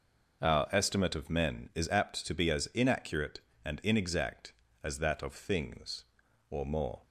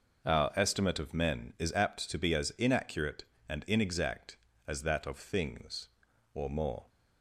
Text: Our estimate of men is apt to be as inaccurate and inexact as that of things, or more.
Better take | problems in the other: neither | none

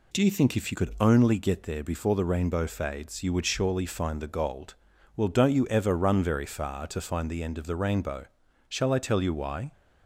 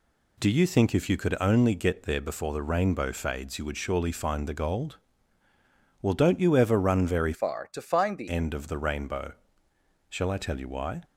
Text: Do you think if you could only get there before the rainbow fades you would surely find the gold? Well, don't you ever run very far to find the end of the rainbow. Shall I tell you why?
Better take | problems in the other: first | changes voice from "far" to "the"; from 7.3 to 8.2 s; 0.9 s long

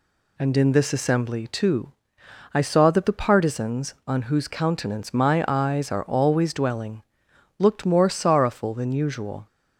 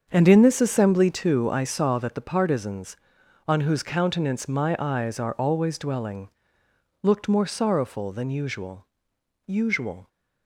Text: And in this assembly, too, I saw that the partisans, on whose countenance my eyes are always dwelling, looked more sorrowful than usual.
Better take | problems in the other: first | starts louder than the rest; until 1.1 s; 7 dB // says "usual" twice; at 9.4 s

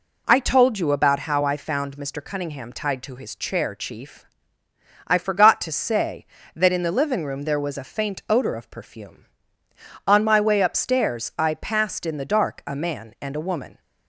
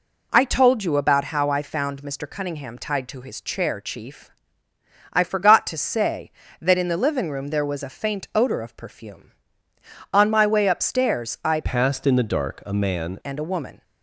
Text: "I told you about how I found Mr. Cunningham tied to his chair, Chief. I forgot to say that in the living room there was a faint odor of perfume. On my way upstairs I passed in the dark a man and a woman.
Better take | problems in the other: first | changes voice from "passed" to "man"; from 11.6 to 13.1 s; 1.5 s long

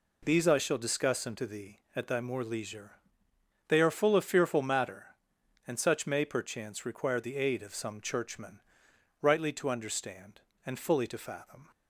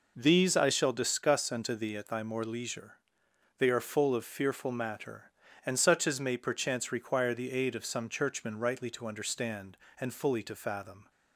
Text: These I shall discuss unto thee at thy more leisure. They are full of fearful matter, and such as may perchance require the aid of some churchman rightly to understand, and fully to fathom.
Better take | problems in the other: second | skips "as"; at 6.0 s // pauses between "churchman" and "rightly"; noticeable; at 8.5 s; 0.60 s long

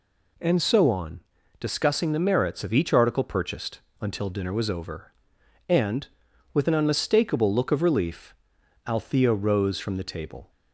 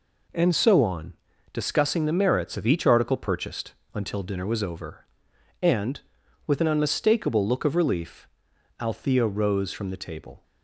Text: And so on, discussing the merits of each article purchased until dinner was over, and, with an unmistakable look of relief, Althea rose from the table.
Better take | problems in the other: first | gets quieter; strong; throughout; 7 dB // pauses between "purchased" and "until"; slight; at 3.7 s; 0.22 s long; slight in the first

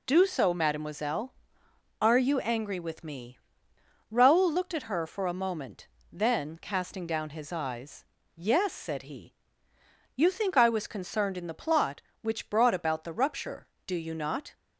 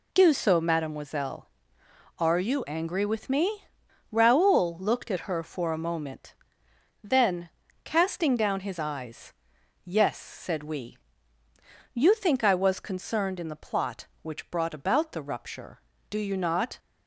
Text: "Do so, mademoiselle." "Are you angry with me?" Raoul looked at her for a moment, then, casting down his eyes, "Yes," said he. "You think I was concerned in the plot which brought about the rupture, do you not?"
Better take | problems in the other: first | says "we" for "he"; at 10.6 s

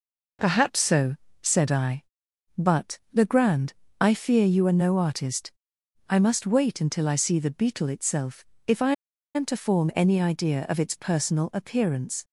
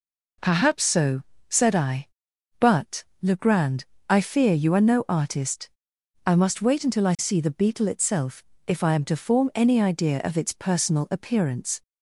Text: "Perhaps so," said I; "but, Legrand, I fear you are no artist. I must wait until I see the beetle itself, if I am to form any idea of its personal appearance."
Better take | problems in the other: second | pauses between "I" and "am"; at 8.9 s; 0.42 s long

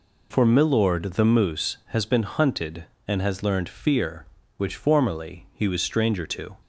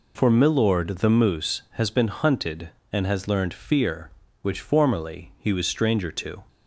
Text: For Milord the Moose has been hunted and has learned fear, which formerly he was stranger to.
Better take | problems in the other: neither | none

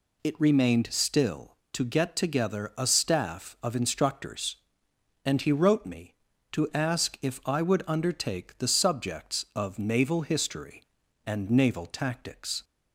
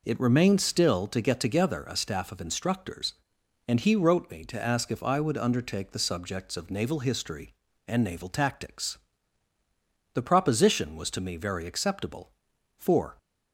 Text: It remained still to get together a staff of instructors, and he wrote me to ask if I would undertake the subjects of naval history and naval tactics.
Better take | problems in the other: first | goes on to say "The proposition was to me very acceptable for"; strong; from 10.1 s on; 3.0 s long

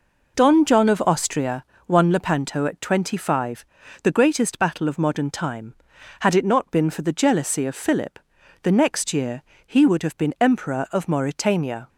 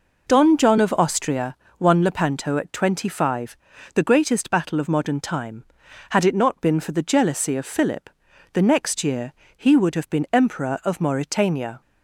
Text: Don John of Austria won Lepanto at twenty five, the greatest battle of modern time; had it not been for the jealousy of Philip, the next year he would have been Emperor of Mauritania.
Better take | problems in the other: neither | pauses between "Austria" and "won"; slight; the same in both // pauses between "year" and "he"; slight; the same in both

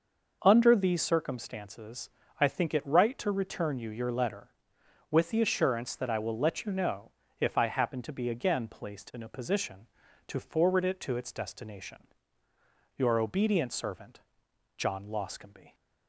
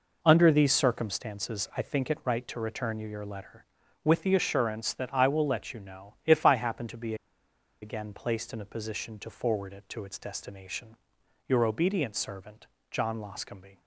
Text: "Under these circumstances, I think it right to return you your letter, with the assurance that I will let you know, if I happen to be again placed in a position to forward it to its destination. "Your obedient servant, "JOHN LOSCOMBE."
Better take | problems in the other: first | pauses between "be" and "again"; noticeable; at 7.1 s; 0.67 s long

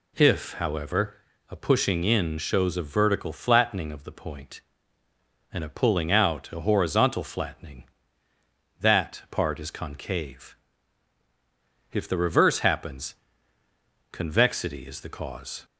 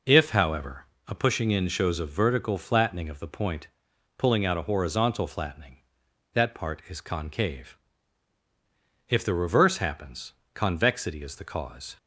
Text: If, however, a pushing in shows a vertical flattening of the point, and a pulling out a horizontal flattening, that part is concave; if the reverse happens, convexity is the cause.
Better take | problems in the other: first | skips "and a"; at 3.9 s

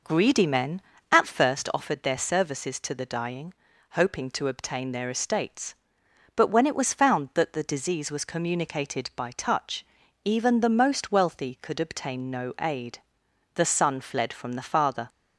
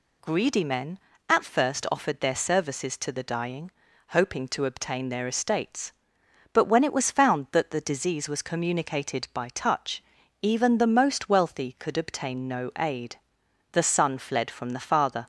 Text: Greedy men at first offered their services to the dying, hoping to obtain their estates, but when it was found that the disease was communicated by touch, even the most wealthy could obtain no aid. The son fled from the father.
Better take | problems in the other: second | starts louder than the rest; noticeable; until 1.7 s; 5 dB

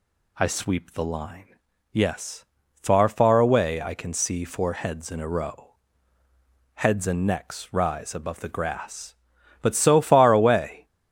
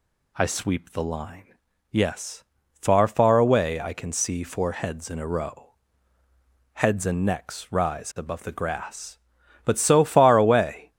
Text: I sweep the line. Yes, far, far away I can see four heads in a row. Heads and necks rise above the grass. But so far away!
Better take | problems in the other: neither | none

